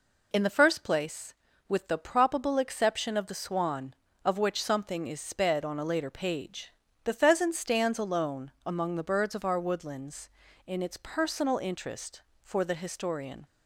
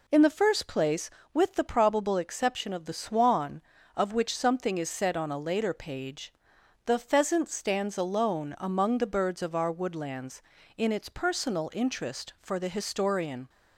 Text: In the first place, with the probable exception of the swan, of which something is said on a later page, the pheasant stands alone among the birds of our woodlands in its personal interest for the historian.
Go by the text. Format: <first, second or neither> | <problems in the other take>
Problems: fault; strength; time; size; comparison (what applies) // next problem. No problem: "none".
second | says "sped" for "said"; at 5.1 s